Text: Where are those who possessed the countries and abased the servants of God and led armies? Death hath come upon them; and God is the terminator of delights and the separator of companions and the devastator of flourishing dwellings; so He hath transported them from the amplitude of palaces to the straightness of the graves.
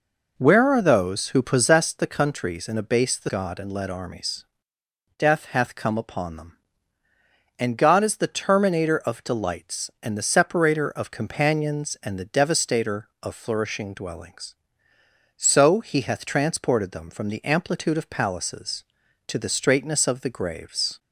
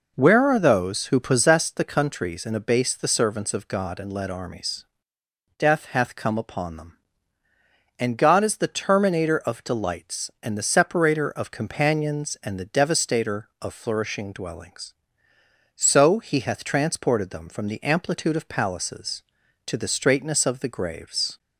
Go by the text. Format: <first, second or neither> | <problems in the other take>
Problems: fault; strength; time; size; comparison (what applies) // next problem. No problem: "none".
second | skips "servants of"; at 3.2 s